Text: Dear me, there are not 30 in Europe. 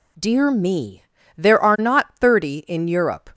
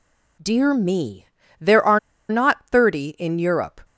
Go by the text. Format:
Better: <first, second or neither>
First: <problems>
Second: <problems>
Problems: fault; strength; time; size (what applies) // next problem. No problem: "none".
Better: first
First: none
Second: pauses between "are" and "not"; slight; at 1.9 s; 0.30 s long